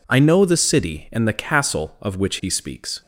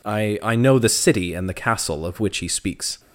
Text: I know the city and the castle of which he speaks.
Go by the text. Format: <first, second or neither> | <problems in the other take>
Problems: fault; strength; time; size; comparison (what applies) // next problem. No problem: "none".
first | says "I" twice; at 0.4 s